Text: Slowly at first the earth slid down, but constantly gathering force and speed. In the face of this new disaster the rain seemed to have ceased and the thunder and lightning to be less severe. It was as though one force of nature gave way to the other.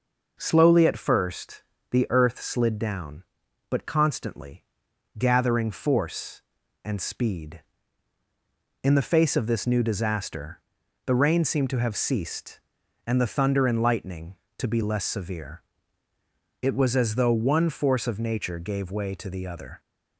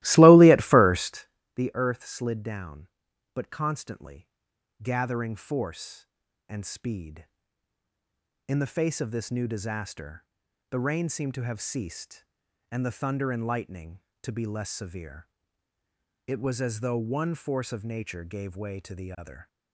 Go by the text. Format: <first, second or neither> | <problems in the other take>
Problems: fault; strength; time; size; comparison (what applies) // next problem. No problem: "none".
first | starts louder than the rest; strong; until 1.4 s; 17.5 dB // pauses between "first" and "the"; slight; at 1.2 s; 0.28 s long; slight in the first // pauses between "constantly" and "gathering"; noticeable; at 4.2 s; 0.56 s long; noticeable in the first // pauses between "disaster" and "the"; noticeable; at 10.2 s; 0.46 s long; noticeable in the first